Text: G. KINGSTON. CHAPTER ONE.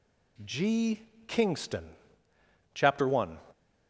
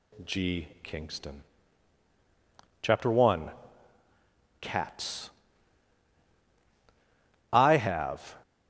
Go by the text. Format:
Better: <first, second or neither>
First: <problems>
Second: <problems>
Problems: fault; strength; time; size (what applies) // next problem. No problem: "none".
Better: first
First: none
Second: goes on to say "CATS I have"; strong; from 4.6 s on; 3.7 s long